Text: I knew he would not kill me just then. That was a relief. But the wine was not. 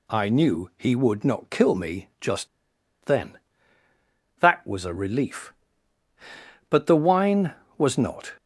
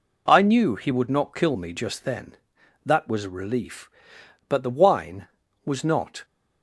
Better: second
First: pauses between "just" and "then"; noticeable; at 2.4 s; 0.57 s long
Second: none

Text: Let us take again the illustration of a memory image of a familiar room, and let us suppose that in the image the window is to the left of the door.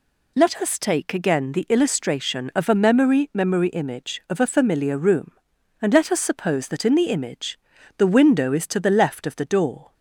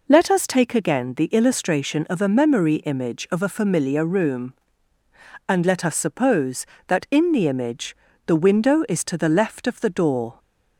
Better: second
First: says "memory" twice; at 3.3 s // pauses between "image" and "the"; at 7.5 s; 0.38 s long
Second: pauses between "image" and "the"; slight; at 7.9 s; 0.30 s long

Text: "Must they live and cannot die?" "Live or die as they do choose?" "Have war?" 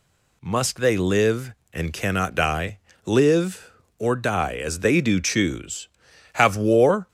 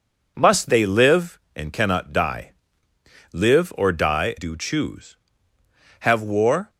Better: first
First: none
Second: skips "as they"; at 4.3 s

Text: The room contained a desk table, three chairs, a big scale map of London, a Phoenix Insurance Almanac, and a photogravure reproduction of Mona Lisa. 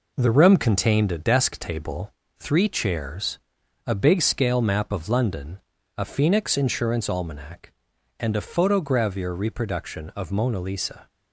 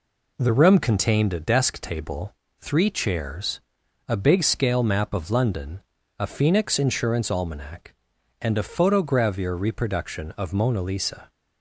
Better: second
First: gets quieter; noticeable; throughout; 5 dB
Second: none

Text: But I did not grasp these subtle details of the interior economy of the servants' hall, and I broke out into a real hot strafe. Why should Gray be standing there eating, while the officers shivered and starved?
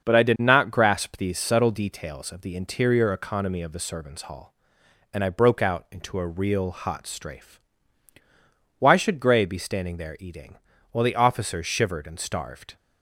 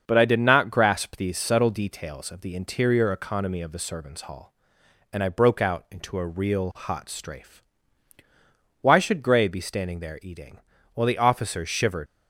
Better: first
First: starts louder than the rest; until 1.0 s; 6.5 dB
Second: starts louder than the rest; until 1.0 s; 7 dB // stops before "and starved"; at 12.0 s

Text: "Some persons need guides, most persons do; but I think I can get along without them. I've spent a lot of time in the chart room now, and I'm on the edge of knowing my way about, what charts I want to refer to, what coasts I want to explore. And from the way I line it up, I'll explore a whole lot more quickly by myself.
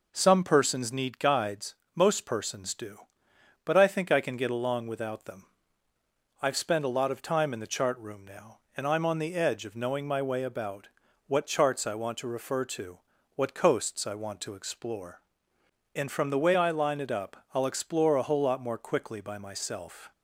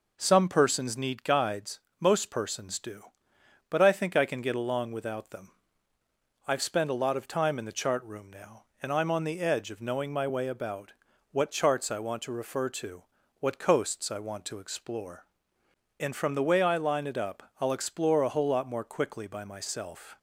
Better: neither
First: none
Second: none

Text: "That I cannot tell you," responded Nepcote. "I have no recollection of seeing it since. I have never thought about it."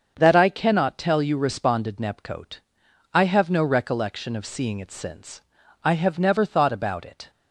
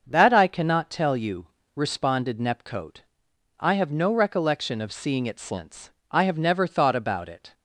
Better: neither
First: starts louder than the rest; until 1.2 s; 7 dB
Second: starts louder than the rest; until 1.0 s; 6.5 dB

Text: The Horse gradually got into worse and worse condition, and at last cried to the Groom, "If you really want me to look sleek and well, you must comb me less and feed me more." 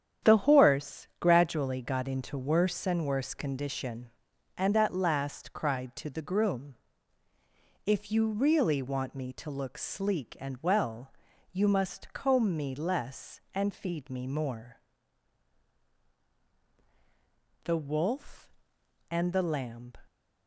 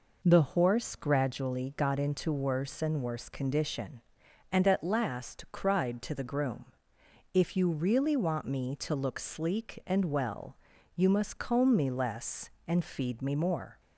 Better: second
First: starts louder than the rest; strong; until 1.3 s; 9 dB // goes on to say "THE WOLF AND THE LAMB"; strong; from 17.6 s on; 2.3 s long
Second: none

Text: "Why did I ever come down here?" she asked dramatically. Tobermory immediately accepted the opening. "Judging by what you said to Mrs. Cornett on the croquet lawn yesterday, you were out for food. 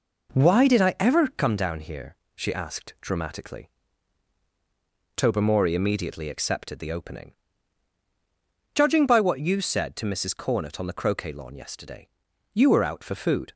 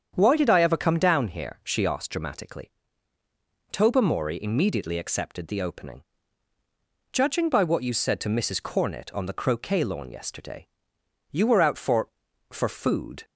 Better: first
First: none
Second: starts louder than the rest; strong; until 1.1 s; 8 dB // says "for" twice; at 12.5 s

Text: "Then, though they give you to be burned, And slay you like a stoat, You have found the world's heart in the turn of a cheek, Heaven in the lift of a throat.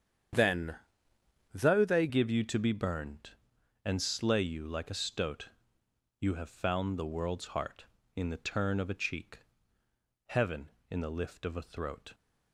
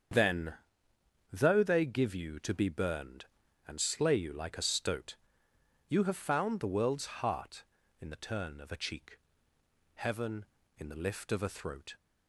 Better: second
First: starts louder than the rest; strong; until 2.0 s; 8.5 dB // changes voice at "give"; from 2.0 s on; 10.1 s long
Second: starts louder than the rest; strong; until 1.8 s; 7.5 dB

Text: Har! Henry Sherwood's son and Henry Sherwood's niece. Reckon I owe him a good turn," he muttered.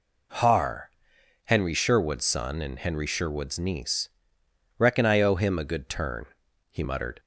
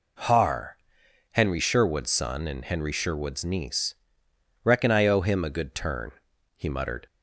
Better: neither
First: none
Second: none

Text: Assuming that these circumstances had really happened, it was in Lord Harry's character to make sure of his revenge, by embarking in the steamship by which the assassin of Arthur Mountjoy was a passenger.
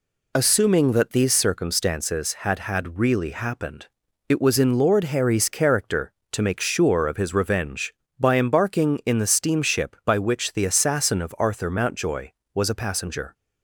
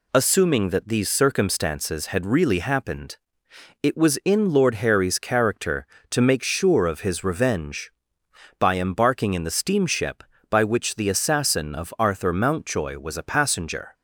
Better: second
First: says "had" twice; at 2.5 s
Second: none

